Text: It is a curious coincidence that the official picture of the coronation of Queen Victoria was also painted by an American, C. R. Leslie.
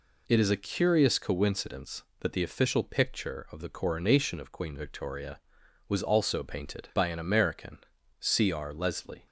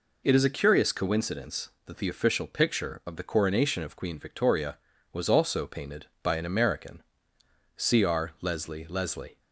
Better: first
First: none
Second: says "Leslie" twice; at 8.8 s

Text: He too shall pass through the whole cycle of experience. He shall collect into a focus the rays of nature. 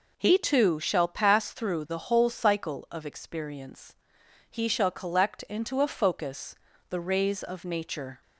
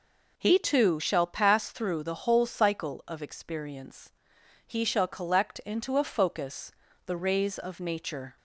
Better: neither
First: pauses between "focus" and "the"; slight; at 6.5 s; 0.34 s long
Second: pauses between "focus" and "the"; slight; at 6.7 s; 0.34 s long

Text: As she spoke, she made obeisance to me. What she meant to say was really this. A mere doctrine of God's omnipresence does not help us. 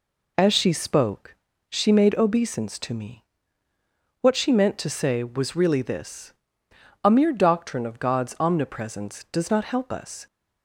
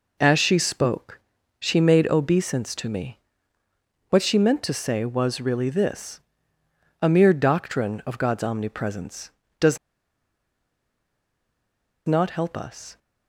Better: first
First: none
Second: pauses between "does" and "not"; strong; at 9.7 s; 2.2 s long

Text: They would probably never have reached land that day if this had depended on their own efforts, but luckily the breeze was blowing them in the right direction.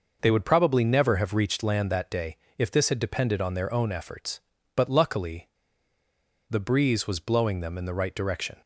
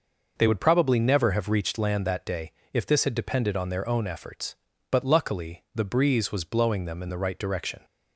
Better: second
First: pauses between "day" and "if"; slight; at 2.3 s; 0.22 s long // pauses between "luckily" and "the"; at 5.4 s; 1.0 s long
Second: pauses between "day" and "if"; slight; at 2.5 s; 0.22 s long

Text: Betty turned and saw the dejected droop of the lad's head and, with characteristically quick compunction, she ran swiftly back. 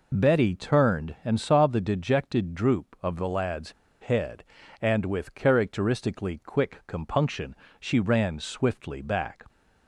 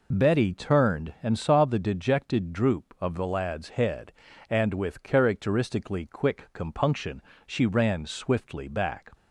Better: second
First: pauses between "lad's" and "head"; slight; at 3.7 s; 0.30 s long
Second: none

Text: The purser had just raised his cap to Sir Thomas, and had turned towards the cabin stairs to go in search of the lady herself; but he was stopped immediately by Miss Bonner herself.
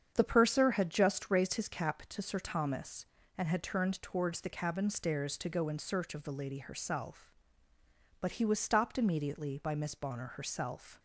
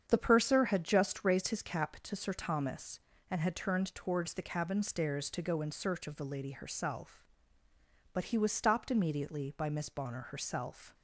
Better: neither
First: starts louder than the rest; strong; until 1.1 s; 8 dB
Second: starts louder than the rest; strong; until 1.0 s; 8 dB

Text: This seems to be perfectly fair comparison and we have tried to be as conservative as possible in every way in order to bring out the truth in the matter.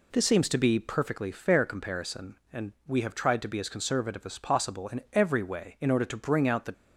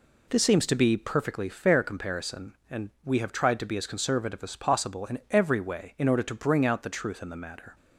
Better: second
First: stops before "truth in the matter"; at 6.7 s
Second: none

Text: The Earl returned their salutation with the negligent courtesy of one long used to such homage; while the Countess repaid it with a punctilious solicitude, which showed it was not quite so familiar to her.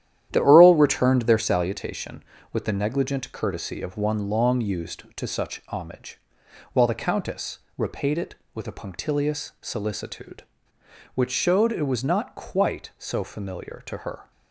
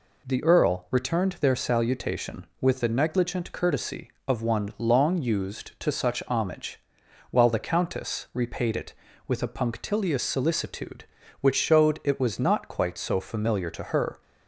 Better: second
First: starts louder than the rest; strong; until 1.7 s; 11 dB // pauses between "Countess" and "repaid"; slight; at 7.5 s; 0.18 s long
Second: none

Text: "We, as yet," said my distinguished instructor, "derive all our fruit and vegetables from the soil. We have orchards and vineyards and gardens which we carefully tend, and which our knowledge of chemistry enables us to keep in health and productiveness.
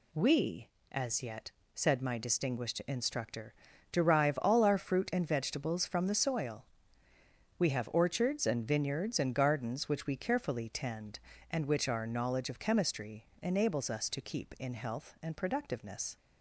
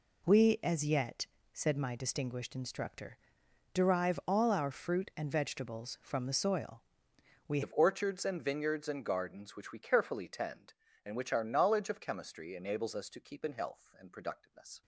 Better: first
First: none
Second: changes voice at "have"; from 7.6 s on; 7.2 s long

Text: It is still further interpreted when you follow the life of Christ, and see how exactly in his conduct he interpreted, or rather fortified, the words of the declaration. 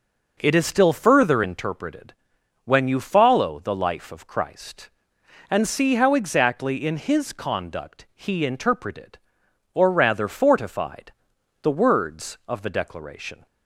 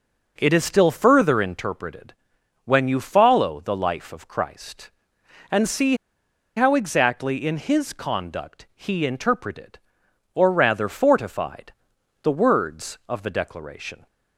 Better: first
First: pauses between "interpreted" and "when"; noticeable; at 2.1 s; 0.52 s long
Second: pauses between "interpreted" and "when"; noticeable; at 2.1 s; 0.52 s long // pauses between "see" and "how"; noticeable; at 5.9 s; 0.61 s long

